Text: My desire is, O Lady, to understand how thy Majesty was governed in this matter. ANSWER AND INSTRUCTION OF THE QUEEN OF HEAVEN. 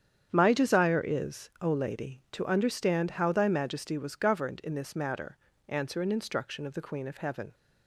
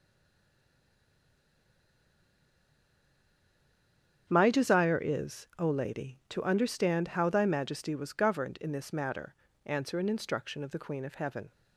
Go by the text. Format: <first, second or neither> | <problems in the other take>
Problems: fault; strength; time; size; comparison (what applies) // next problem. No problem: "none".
first | stays silent before the first word; strong; until 4.2 s; 4.2 s long // starts louder than the rest; strong; until 5.3 s; 8.5 dB; strong in the first